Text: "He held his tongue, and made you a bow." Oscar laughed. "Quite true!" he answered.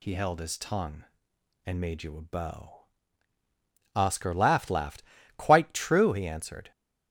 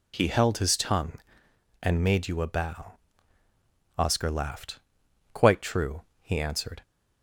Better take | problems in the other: second | says "laughed" twice; at 4.6 s

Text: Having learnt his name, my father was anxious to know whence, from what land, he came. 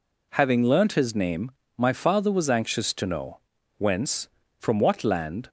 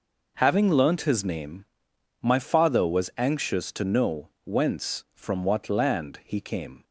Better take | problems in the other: second | pauses between "know" and "whence"; noticeable; at 3.3 s; 0.46 s long; slight in the second // stops before "he came"; at 5.4 s

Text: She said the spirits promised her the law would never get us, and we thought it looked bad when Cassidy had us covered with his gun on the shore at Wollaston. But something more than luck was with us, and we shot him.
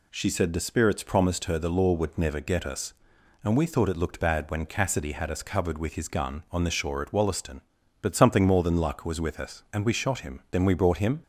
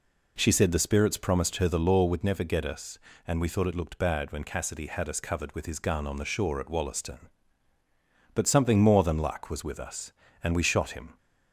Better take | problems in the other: second | goes on to say "Then we brought him"; noticeable; from 10.5 s on; 0.72 s long

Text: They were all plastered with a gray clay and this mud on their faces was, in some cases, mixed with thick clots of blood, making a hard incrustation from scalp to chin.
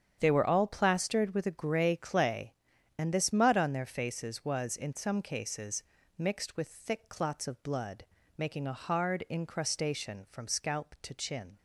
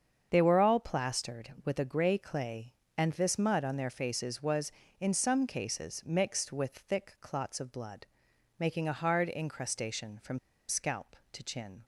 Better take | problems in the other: first | starts louder than the rest; strong; until 1.3 s; 7 dB; strong in the first // pauses between "from" and "scalp"; slight; at 10.3 s; 0.29 s long

